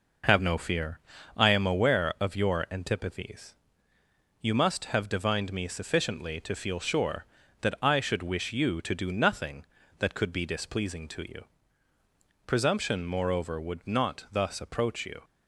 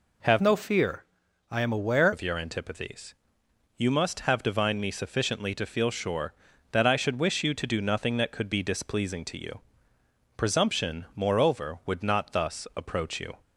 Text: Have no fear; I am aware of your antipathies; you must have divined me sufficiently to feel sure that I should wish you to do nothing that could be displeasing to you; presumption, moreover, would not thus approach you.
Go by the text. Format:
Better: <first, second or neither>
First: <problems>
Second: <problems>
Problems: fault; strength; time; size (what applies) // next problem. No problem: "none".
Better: first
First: none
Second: changes voice from "no" to "aware"; from 0.4 to 2.1 s; 1.7 s long